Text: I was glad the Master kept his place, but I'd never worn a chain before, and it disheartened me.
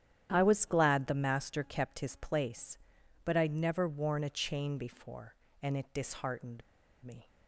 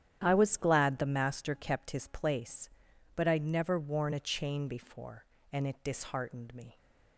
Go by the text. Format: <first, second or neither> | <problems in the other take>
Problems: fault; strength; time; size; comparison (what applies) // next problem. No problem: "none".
second | starts louder than the rest; strong; until 1.3 s; 10.5 dB; strong in the second // pauses between "disheartened" and "me"; at 6.6 s; 0.41 s long